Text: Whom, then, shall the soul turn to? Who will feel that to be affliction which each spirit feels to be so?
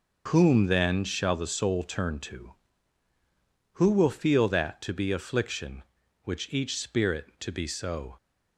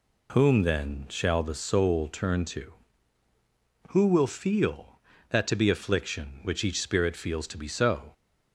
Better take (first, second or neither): second